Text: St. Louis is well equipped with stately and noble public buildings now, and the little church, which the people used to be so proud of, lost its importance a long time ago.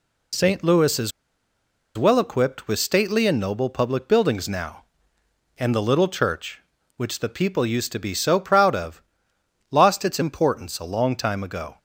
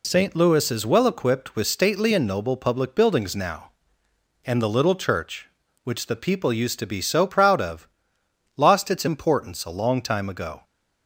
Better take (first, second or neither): second